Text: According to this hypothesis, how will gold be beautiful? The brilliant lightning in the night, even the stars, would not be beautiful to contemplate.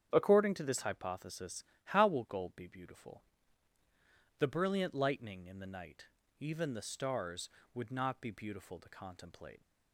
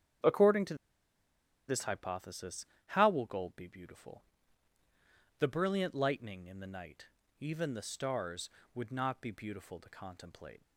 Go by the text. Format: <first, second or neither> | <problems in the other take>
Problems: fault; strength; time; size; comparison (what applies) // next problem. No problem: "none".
first | starts louder than the rest; strong; until 2.1 s; 8.5 dB; strong in the first // pauses between "to" and "this"; noticeable; at 0.7 s; 0.93 s long